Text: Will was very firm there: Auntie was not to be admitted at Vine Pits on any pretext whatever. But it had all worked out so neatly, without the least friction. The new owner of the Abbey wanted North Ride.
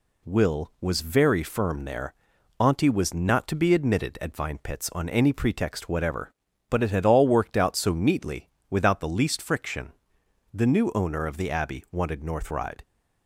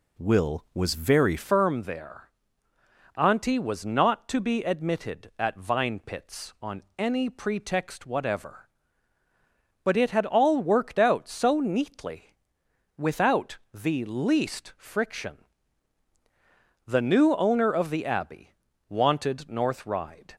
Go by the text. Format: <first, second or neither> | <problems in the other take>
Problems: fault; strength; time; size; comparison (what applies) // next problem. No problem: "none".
first | changes voice at "firm"; from 1.3 s on; 19.0 s long // pauses between "without" and "the"; slight; at 13.5 s; 0.16 s long // pauses between "Abbey" and "wanted"; at 18.5 s; 0.38 s long